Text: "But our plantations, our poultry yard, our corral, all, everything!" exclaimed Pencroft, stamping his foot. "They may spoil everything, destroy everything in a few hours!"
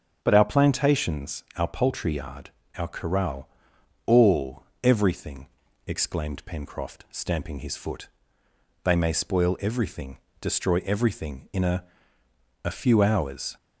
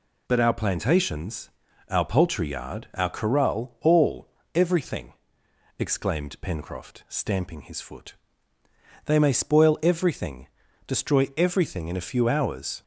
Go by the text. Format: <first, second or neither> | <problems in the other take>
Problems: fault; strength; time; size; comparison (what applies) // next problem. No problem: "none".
second | starts louder than the rest; until 1.2 s; 7 dB // says "a" twice; at 12.6 s